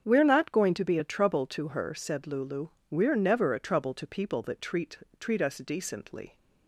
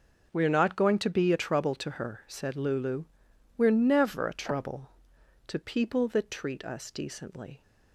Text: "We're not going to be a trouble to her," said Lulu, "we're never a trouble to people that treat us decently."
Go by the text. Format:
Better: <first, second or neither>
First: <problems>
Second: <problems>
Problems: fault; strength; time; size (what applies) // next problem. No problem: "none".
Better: second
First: starts louder than the rest; strong; until 1.0 s; 7.5 dB // says "treat" twice; at 5.2 s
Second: starts louder than the rest; until 1.3 s; 6.5 dB